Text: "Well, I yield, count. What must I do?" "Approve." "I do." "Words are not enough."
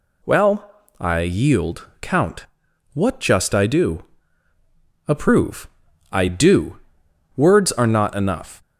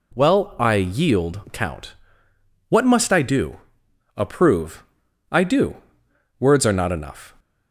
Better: second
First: says "just" for "must"; at 3.2 s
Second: none

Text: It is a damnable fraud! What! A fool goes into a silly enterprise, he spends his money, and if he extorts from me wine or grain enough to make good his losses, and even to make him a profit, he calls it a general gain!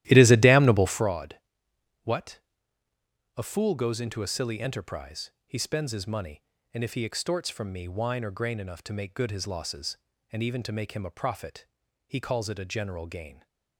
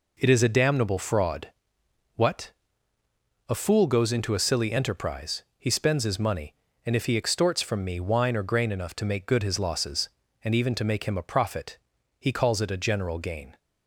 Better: second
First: starts louder than the rest; strong; until 1.1 s; 14 dB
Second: none

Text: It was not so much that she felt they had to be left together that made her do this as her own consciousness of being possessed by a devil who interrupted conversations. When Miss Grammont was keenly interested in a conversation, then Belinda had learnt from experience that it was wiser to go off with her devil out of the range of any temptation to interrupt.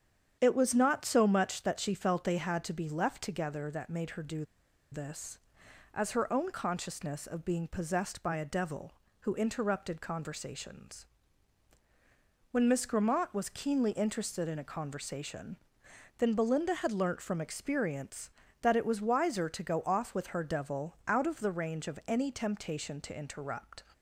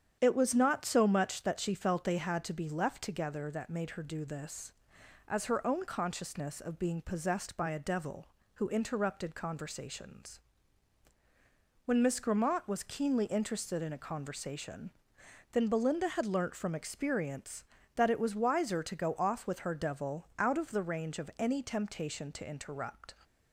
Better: second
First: starts louder than the rest; strong; until 1.4 s; 8.5 dB // pauses between "do" and "this"; noticeable; at 4.4 s; 0.47 s long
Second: starts louder than the rest; strong; until 1.2 s; 8.5 dB

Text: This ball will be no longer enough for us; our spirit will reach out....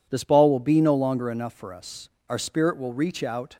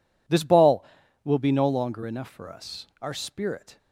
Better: first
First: none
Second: stops before "will reach out"; at 3.7 s

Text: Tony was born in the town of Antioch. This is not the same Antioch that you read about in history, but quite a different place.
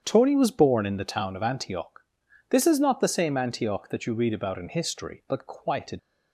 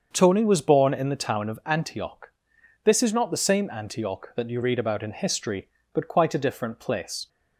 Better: second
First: starts louder than the rest; strong; until 1.0 s; 8 dB // stops before "different place"; at 5.9 s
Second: starts louder than the rest; until 1.1 s; 6.5 dB

